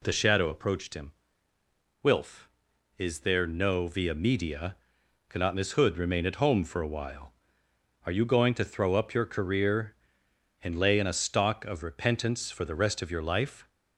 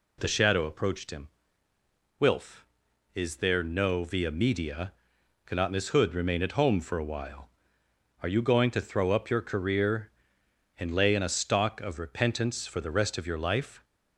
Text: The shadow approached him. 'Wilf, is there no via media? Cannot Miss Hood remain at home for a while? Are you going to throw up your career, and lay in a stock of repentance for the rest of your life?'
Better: neither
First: none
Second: none

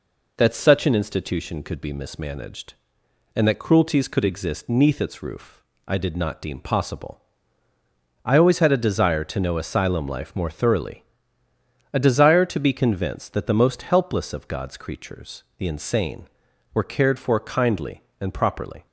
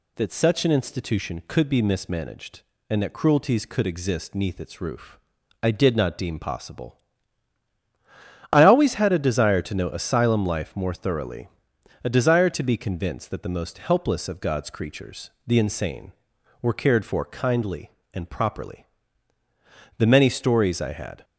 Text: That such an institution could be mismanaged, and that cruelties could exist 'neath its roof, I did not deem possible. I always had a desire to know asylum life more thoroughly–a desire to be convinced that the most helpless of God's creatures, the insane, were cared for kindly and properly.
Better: first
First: none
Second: goes on to say "The many stories I had"; noticeable; from 19.9 s on; 1.2 s long

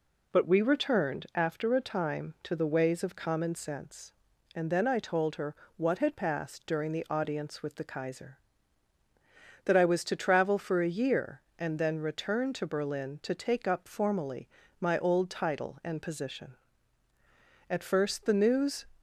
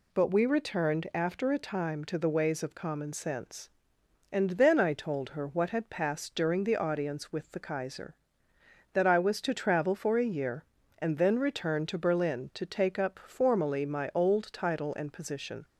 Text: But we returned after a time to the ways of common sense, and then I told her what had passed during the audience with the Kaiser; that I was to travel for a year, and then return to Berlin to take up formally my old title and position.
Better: second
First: pauses between "her" and "what"; slight; at 5.5 s; 0.22 s long // pauses between "formally" and "my"; slight; at 14.4 s; 0.32 s long // goes on to say "At first the news"; noticeable; from 17.6 s on; 1.1 s long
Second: none

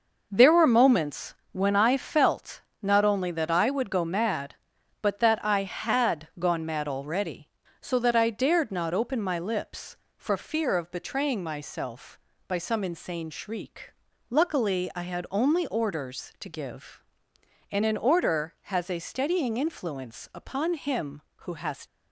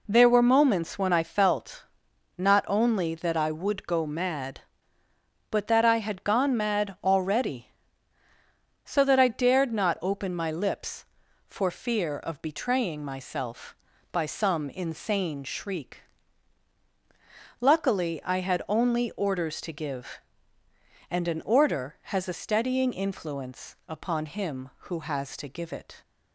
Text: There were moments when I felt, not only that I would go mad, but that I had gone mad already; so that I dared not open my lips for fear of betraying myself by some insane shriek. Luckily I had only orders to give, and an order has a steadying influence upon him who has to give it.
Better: second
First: pauses between "moments" and "when"; slight; at 1.3 s; 0.20 s long // stops before "to give it"; at 21.8 s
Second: none

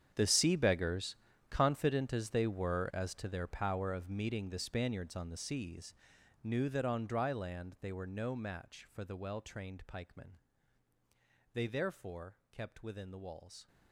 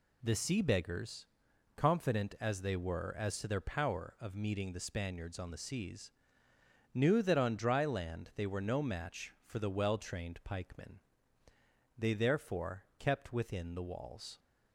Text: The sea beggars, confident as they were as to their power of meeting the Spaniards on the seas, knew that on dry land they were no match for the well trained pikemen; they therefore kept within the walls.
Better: second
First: gets quieter; strong; throughout; 16.5 dB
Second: none

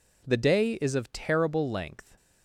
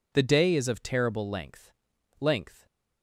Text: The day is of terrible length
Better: first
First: none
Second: says "length" twice; at 2.1 s

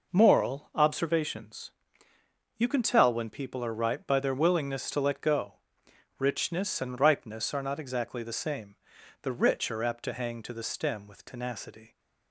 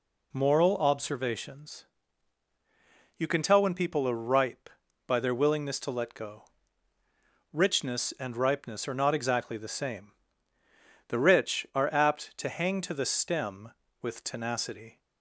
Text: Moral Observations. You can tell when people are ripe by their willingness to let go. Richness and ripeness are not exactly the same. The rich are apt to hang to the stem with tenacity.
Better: neither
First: none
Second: none

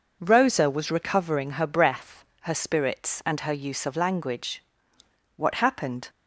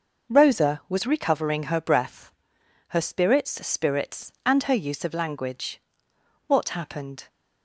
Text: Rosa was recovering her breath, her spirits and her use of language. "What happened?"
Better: first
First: none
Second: says "spirits" twice; at 3.6 s

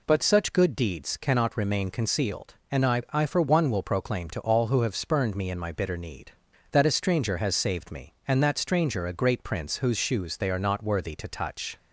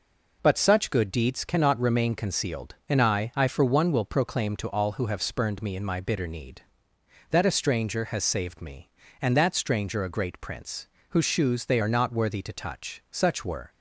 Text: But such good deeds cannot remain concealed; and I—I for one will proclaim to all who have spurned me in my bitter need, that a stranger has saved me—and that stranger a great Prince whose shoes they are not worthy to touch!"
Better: first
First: none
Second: pauses between "Prince" and "whose"; slight; at 10.8 s; 0.24 s long // goes on to say "Such were"; from 13.0 s on; 0.60 s long

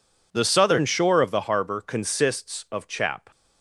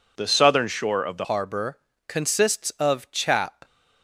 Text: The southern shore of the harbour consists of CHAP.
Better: first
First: none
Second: changes voice at "harbour"; from 1.2 s on; 2.4 s long // pauses between "harbour" and "consists"; slight; at 1.7 s; 0.28 s long

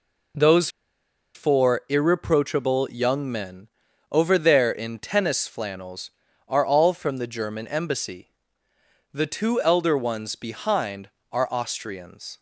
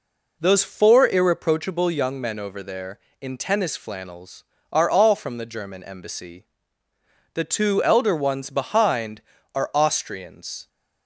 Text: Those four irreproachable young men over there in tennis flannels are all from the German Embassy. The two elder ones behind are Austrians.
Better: second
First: pauses between "Those" and "four"; noticeable; at 0.6 s; 0.66 s long // pauses between "men" and "over"; at 3.6 s; 0.44 s long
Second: none

